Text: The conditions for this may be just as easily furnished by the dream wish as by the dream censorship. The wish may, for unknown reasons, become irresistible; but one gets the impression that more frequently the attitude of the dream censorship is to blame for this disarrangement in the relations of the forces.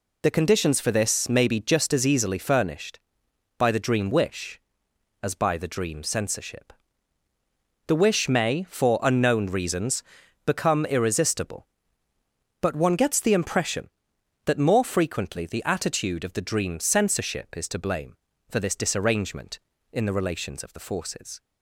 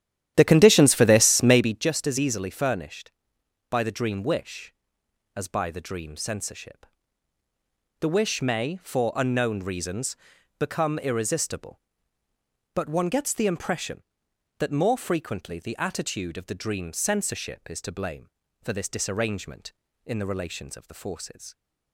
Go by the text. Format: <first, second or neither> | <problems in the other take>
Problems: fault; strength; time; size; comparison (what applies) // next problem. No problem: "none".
first | starts louder than the rest; strong; until 1.8 s; 11.5 dB